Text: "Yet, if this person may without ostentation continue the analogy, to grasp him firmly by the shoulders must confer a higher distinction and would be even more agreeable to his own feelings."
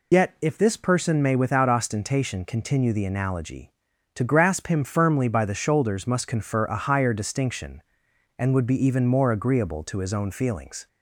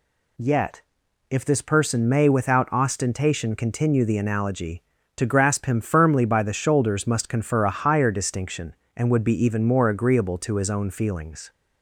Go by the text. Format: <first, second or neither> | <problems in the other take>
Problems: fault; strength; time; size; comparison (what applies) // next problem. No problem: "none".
second | loses the start of "Yet"; at 0.1 s; 65 ms